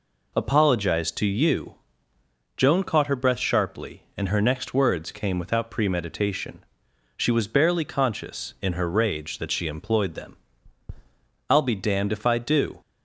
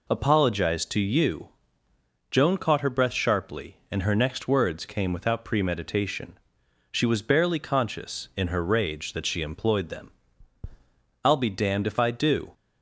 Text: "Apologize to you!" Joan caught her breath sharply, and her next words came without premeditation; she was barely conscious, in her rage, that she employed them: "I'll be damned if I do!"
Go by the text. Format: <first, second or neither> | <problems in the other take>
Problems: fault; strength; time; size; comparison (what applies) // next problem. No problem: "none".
neither | none